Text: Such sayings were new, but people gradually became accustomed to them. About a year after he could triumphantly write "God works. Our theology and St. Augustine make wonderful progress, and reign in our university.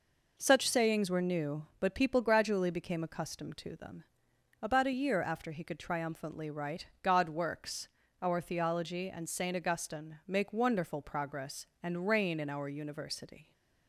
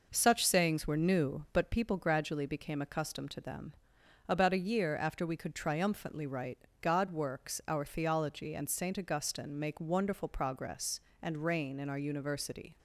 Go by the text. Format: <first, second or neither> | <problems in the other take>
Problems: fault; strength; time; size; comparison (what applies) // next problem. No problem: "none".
first | says "we" for "he"; at 5.2 s // pauses between "write" and "God"; slight; at 6.6 s; 0.16 s long; slight in the first